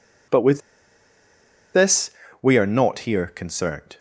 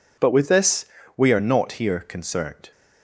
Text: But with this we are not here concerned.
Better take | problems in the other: second | pauses between "with" and "this"; at 0.6 s; 1.1 s long // pauses between "this" and "we"; slight; at 2.1 s; 0.28 s long; slight in the second

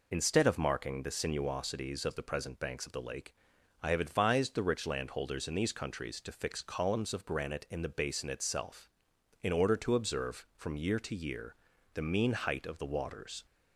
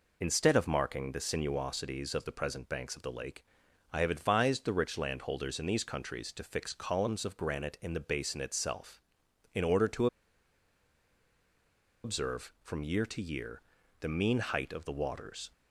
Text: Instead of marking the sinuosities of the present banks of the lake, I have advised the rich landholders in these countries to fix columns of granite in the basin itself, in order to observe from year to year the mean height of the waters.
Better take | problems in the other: first | pauses between "to" and "observe"; strong; at 10.0 s; 1.9 s long // pauses between "year" and "the"; at 13.6 s; 0.38 s long; also in the first

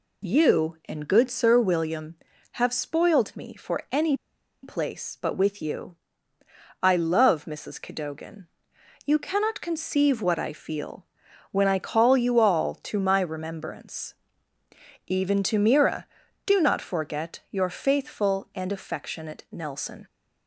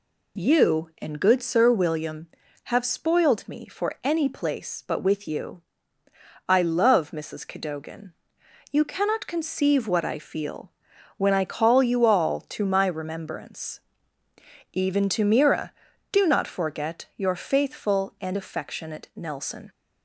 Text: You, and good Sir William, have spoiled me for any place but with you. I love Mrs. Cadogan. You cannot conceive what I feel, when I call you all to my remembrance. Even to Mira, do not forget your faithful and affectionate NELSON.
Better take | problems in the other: second | pauses between "any" and "place"; noticeable; at 4.1 s; 0.47 s long

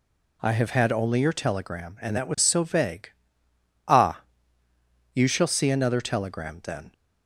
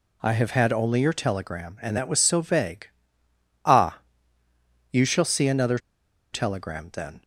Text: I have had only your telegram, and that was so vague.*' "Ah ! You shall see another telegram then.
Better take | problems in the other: first | pauses between "another" and "telegram"; noticeable; at 5.7 s; 0.54 s long

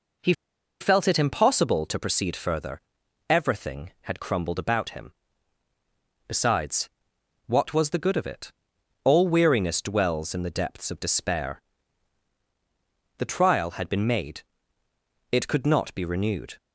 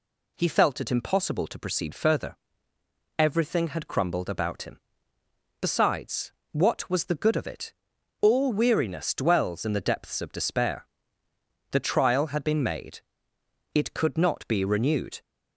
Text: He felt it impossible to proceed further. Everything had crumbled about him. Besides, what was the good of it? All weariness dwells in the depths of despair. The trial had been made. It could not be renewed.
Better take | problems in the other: second | pauses between "He" and "felt"; noticeable; at 0.3 s; 0.47 s long

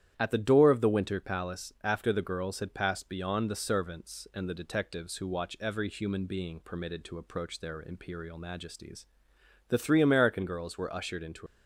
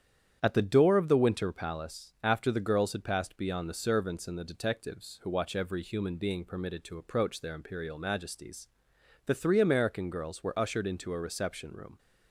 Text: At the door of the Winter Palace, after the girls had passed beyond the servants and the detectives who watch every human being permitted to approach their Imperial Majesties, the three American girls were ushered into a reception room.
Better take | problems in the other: second | starts louder than the rest; strong; until 1.1 s; 10.5 dB; strong in the second // stops before "a reception room"; at 11.4 s

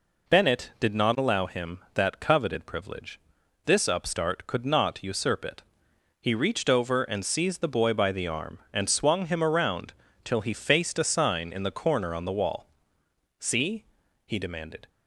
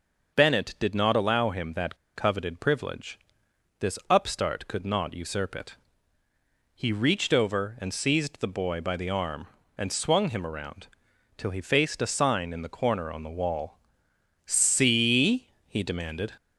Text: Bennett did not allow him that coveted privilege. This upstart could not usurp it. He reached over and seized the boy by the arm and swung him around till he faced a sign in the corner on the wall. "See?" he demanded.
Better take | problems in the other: first | pauses between "that" and "coveted"; slight; at 1.9 s; 0.19 s long // pauses between "around" and "till"; noticeable; at 10.8 s; 0.50 s long; slight in the first

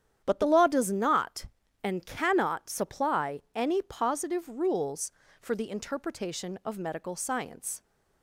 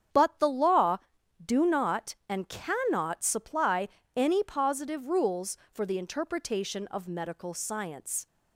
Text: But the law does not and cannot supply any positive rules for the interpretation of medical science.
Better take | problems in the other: first | starts louder than the rest; strong; until 1.5 s; 8.5 dB; strong in the first // says "do" for "does"; at 1.4 s // pauses between "supply" and "any"; slight; at 3.8 s; 0.28 s long

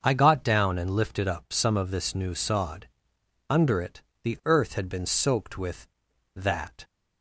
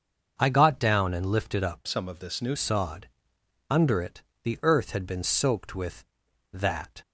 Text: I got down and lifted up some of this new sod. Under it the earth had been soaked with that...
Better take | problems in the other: first | starts louder than the rest; until 1.3 s; 6.5 dB; also in the first // changes voice from "some" to "new"; from 1.8 to 2.5 s; 0.7 s long // pauses between "it" and "the"; slight; at 4.2 s; 0.22 s long; slight in the first

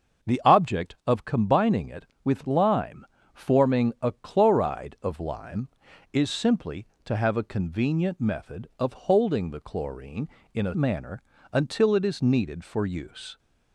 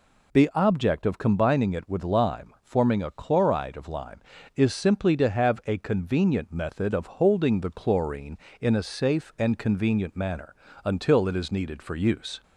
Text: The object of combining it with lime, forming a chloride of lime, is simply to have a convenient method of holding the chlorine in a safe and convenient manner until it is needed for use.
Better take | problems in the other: second | starts louder than the rest; until 1.4 s; 6.5 dB // skips "safe and convenient"; at 10.7 s // pauses between "manner" and "until"; slight; at 11.2 s; 0.28 s long; slight in the second

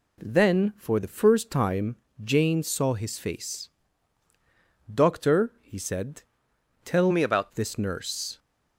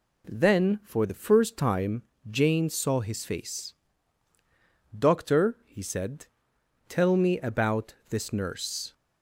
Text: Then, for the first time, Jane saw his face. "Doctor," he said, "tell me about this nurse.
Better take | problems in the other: second | changes voice from "me" to "about"; from 7.1 to 7.5 s; 0.4 s long

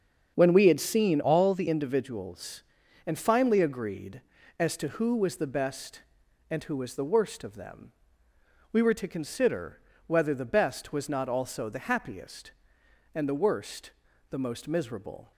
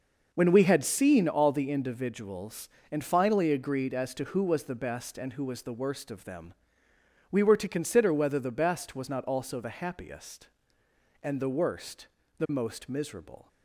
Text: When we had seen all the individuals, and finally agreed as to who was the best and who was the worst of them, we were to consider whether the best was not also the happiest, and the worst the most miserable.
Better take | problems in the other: second | starts louder than the rest; until 1.3 s; 7 dB // changes voice from "all" to "the"; from 1.2 to 1.6 s; 0.4 s long // pauses between "consider" and "whether"; slight; at 9.7 s; 0.28 s long // pauses between "worst" and "the"; at 13.9 s; 0.38 s long; slight in the second

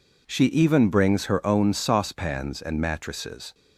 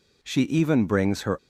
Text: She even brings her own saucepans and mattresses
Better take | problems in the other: first | stops before "own saucepans and mattresses"; at 1.3 s

